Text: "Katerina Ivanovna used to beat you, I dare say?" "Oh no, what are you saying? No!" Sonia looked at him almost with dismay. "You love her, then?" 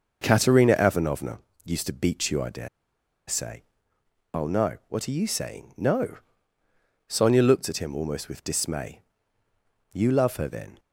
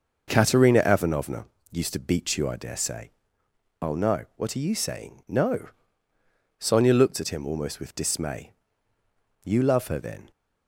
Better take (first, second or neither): second